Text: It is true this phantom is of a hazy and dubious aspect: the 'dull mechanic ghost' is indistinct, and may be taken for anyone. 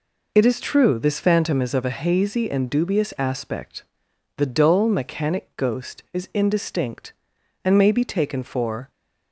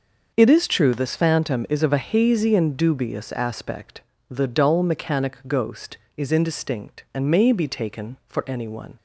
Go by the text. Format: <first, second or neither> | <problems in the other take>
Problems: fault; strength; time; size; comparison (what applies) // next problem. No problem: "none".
second | stops before "anyone"; at 8.9 s